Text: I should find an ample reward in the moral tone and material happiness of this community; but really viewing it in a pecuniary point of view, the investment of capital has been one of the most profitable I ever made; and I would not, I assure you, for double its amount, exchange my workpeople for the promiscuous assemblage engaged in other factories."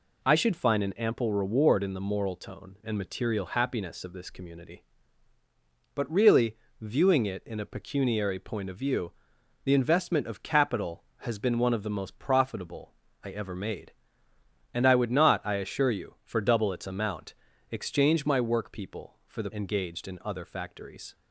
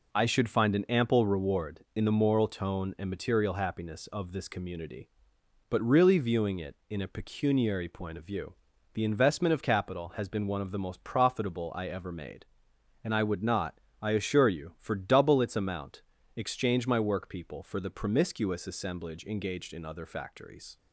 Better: second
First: pauses between "really" and "viewing"; slight; at 6.5 s; 0.24 s long // pauses between "profitable" and "I"; slight; at 12.9 s; 0.30 s long // skips "promiscuous assemblage"; at 19.5 s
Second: none

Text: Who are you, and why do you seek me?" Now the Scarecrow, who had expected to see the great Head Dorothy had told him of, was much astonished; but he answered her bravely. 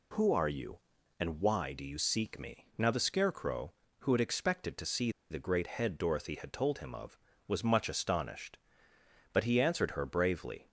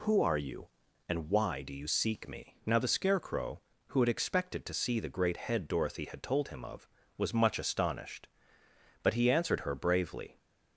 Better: second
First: pauses between "see" and "the"; slight; at 5.0 s; 0.20 s long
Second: none

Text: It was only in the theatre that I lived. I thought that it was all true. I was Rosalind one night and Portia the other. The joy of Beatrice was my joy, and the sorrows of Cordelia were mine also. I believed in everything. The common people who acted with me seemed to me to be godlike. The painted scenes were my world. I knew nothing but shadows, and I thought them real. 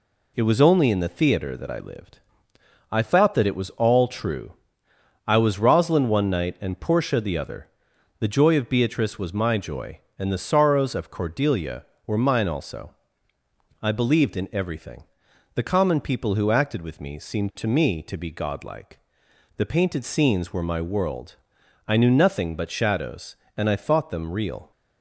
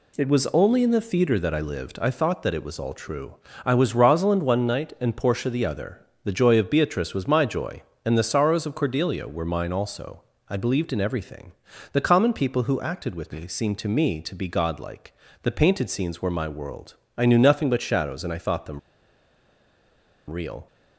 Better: first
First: none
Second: pauses between "them" and "real"; strong; at 18.7 s; 1.5 s long

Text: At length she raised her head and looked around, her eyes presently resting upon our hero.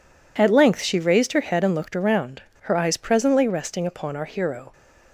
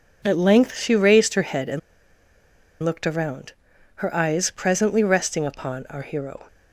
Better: first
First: none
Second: pauses between "and" and "looked"; at 1.7 s; 1.0 s long

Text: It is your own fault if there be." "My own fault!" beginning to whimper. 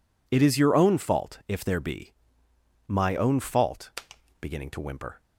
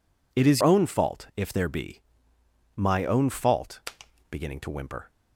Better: first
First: none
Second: skips "your"; at 0.6 s

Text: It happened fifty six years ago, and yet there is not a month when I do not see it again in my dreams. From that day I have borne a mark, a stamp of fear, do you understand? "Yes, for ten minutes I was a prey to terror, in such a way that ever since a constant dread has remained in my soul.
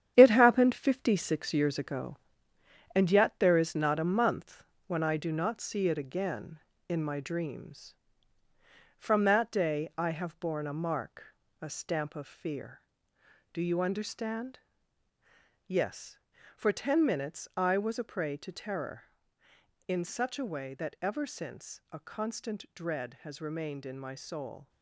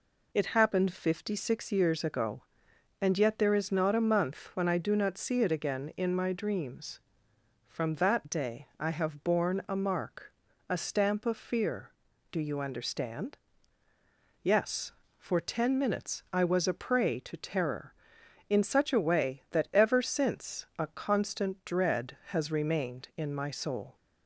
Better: second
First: gets quieter; strong; throughout; 8 dB // pauses between "month" and "when"; slight; at 4.6 s; 0.24 s long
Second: none

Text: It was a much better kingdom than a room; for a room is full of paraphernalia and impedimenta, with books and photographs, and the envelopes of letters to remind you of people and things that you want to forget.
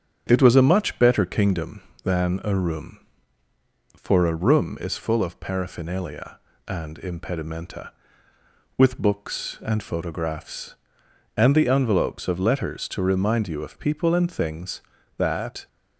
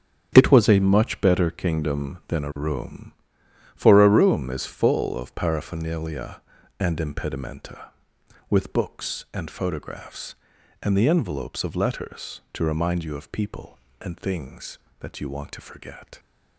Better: second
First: starts louder than the rest; strong; until 1.2 s; 8.5 dB // stops before "you want to forget"; at 15.6 s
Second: starts louder than the rest; strong; until 1.3 s; 8.5 dB

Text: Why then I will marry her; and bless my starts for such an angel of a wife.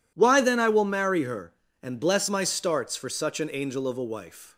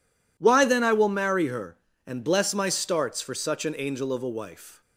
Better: neither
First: none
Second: none

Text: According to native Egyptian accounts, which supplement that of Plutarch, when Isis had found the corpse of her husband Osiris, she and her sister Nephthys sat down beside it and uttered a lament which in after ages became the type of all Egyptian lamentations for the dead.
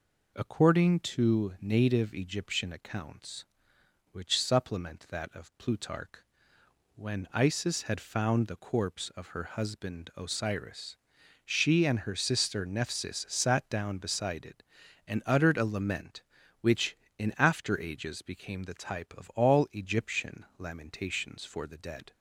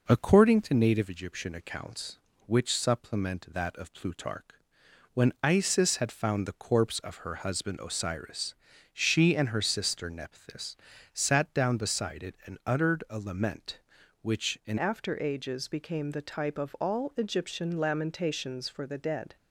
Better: first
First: none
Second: pauses between "Nephthys" and "sat"; slight; at 10.7 s; 0.36 s long // changes voice at "after"; from 14.7 s on; 4.6 s long

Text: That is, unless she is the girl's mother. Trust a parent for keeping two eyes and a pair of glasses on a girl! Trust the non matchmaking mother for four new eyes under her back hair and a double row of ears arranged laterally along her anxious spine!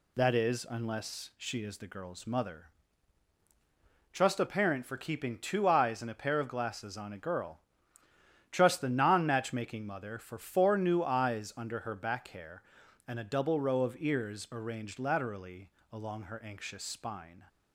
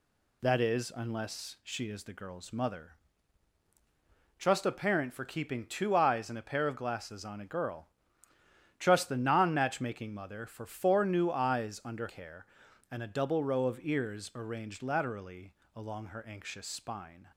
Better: first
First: pauses between "laterally" and "along"; slight; at 15.7 s; 0.20 s long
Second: skips "her back"; at 12.0 s // pauses between "laterally" and "along"; slight; at 15.5 s; 0.20 s long

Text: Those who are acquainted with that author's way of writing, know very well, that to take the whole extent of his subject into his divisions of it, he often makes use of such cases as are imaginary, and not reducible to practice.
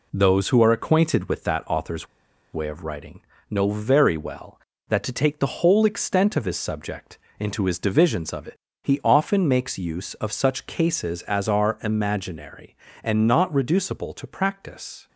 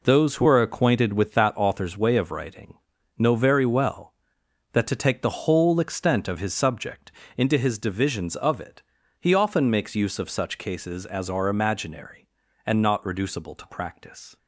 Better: second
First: pauses between "author's" and "way"; noticeable; at 2.0 s; 0.46 s long // pauses between "subject" and "into"; slight; at 7.1 s; 0.20 s long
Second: pauses between "subject" and "into"; slight; at 7.1 s; 0.24 s long

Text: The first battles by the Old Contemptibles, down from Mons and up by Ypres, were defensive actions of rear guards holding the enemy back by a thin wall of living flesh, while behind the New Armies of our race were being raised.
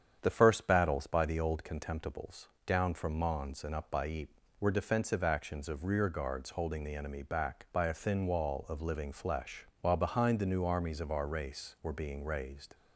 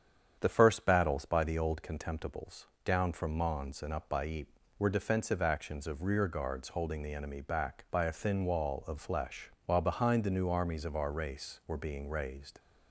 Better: first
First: starts louder than the rest; strong; until 1.2 s; 8.5 dB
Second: starts louder than the rest; strong; until 1.4 s; 8.5 dB // skips "living"; at 8.9 s

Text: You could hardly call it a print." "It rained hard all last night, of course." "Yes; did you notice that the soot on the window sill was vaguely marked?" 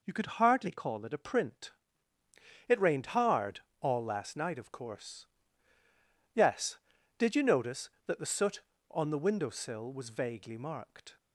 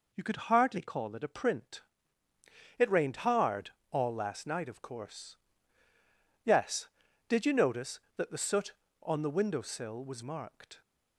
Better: first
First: pauses between "hard" and "all"; slight; at 3.5 s; 0.20 s long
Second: pauses between "hard" and "all"; slight; at 3.7 s; 0.20 s long // skips "vaguely"; at 10.2 s

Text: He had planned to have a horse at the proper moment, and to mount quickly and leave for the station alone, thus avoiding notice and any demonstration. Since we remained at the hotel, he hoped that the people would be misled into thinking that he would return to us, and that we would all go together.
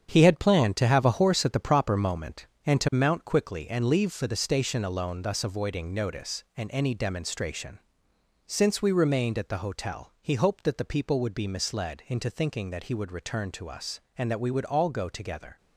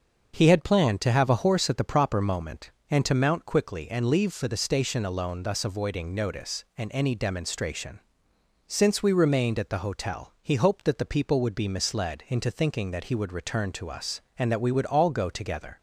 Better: second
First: gets quieter; strong; throughout; 8 dB // starts louder than the rest; strong; until 1.1 s; 8 dB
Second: starts louder than the rest; until 1.3 s; 6.5 dB

